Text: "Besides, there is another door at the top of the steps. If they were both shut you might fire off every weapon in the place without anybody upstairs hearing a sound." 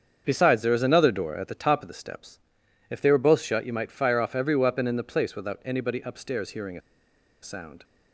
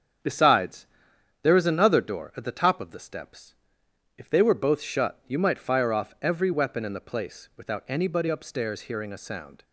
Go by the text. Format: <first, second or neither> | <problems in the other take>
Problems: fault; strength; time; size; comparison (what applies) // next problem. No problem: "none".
second | starts louder than the rest; strong; until 1.2 s; 7 dB; strong in the second // pauses between "a" and "sound"; noticeable; at 6.8 s; 0.62 s long